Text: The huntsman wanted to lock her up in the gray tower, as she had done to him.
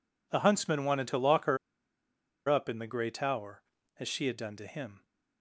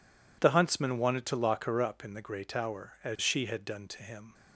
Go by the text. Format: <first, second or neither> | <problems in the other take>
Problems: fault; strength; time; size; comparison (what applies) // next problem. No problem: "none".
second | pauses between "her" and "up"; noticeable; at 1.5 s; 0.91 s long